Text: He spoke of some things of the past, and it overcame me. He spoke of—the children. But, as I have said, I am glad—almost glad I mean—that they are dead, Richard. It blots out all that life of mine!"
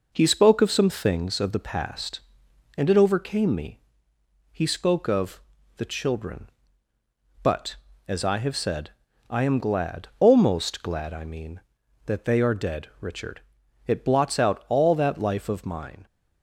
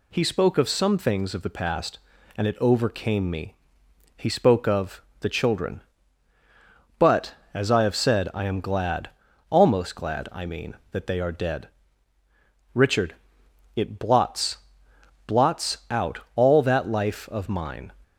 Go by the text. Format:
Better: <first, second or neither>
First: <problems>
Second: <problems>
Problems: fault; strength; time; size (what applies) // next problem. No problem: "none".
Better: first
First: none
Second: says "blots" twice; at 15.2 s